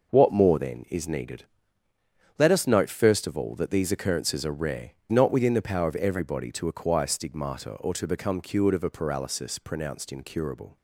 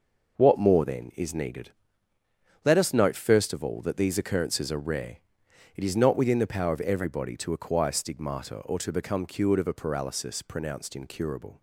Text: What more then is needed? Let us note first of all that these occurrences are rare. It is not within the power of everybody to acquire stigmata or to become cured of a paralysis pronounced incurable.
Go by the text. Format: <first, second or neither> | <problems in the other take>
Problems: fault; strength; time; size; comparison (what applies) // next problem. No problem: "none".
second | skips "It is"; at 5.0 s